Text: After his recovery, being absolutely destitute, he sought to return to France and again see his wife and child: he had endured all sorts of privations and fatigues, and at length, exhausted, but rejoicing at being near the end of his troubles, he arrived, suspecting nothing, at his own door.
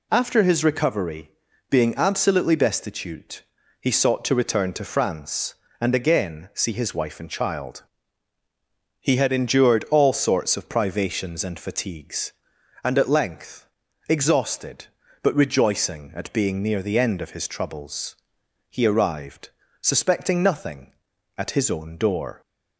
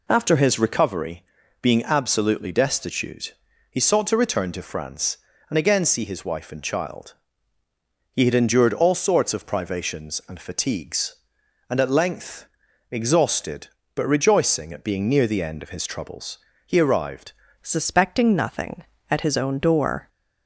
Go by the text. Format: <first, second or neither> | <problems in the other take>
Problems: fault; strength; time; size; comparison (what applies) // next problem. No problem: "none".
first | changes voice at "suspecting"; from 17.6 s on; 2.4 s long